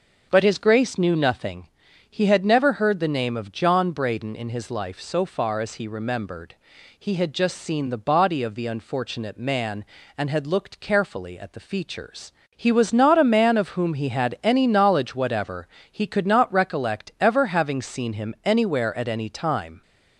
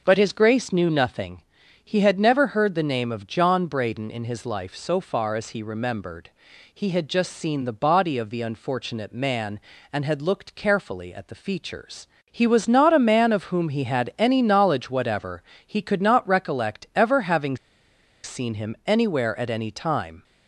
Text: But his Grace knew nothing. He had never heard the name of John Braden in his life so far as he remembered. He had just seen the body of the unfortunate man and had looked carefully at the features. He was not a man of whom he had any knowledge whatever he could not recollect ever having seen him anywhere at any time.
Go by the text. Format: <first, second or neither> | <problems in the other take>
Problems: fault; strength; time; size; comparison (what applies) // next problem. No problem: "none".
first | starts louder than the rest; noticeable; until 1.0 s; 6 dB; also in the first // pauses between "whatever" and "he"; slight; at 15.4 s; 0.22 s long; slight in the first // pauses between "having" and "seen"; noticeable; at 17.5 s; 0.68 s long